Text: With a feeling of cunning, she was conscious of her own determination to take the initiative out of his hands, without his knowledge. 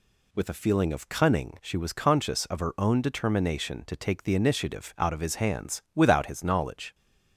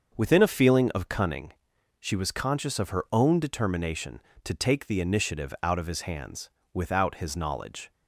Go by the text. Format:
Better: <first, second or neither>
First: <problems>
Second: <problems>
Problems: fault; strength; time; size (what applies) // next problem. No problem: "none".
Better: first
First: none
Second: starts louder than the rest; until 1.1 s; 6.5 dB // says "Within" for "With"; at 0.1 s